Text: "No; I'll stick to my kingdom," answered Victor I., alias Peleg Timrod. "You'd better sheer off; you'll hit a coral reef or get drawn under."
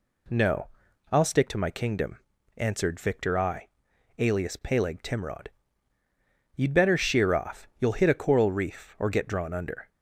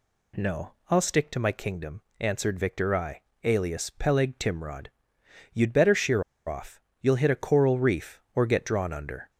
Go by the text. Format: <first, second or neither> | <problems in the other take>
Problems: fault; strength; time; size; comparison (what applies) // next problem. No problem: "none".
first | pauses between "sheer" and "off"; slight; at 6.2 s; 0.25 s long